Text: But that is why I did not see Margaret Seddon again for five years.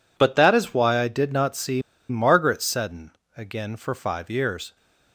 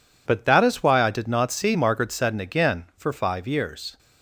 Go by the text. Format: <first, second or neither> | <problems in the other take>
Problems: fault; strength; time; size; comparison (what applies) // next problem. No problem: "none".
second | pauses between "see" and "Margaret"; slight; at 1.8 s; 0.27 s long // pauses between "Seddon" and "again"; slight; at 3.1 s; 0.24 s long